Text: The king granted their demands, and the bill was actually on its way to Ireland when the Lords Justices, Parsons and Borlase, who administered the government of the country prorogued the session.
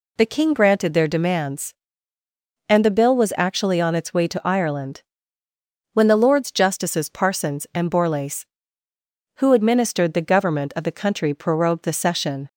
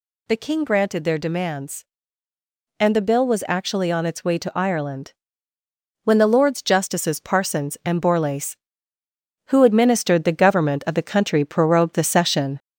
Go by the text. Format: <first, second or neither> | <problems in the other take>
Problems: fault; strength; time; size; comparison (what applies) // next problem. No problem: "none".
first | gets louder; slight; throughout; 2.5 dB // pauses between "Ireland" and "when"; noticeable; at 5.1 s; 0.92 s long; noticeable in the first